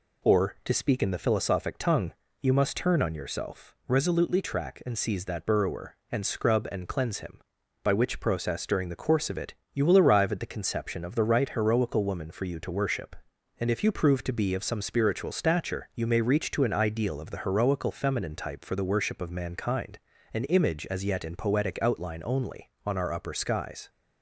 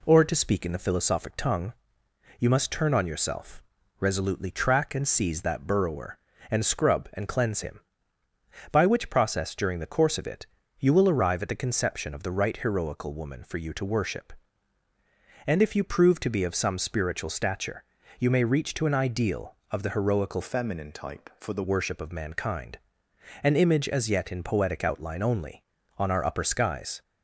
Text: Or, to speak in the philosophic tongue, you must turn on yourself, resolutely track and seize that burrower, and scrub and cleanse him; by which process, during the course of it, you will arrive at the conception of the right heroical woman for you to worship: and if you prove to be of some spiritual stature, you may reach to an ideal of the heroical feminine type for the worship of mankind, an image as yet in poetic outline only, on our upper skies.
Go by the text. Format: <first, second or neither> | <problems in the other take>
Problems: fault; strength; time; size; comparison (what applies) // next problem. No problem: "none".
first | changes voice from "feminine" to "the"; from 20.4 to 21.6 s; 1.2 s long